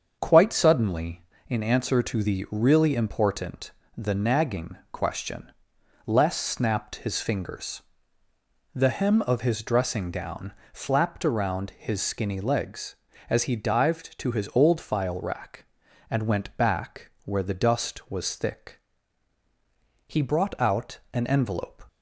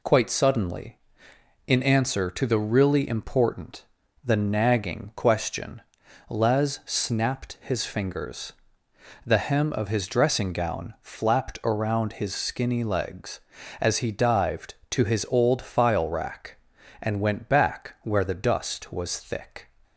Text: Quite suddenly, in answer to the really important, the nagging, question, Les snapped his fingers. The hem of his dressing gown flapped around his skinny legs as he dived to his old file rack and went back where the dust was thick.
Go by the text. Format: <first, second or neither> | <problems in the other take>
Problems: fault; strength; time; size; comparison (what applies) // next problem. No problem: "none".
second | starts louder than the rest; until 1.2 s; 7 dB // pauses between "gown" and "flapped"; slight; at 10.5 s; 0.20 s long // goes on to say "He brought out an envelope"; strong; from 20.0 s on; 1.7 s long